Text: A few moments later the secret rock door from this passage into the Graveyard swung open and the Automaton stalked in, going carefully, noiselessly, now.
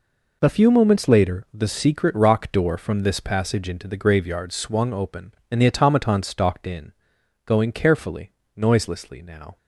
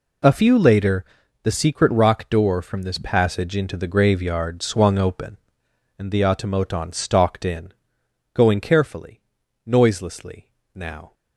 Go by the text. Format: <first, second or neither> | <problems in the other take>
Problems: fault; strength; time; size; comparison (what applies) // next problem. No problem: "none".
first | skips "moments"; at 0.5 s // pauses between "later" and "the"; at 1.0 s; 0.38 s long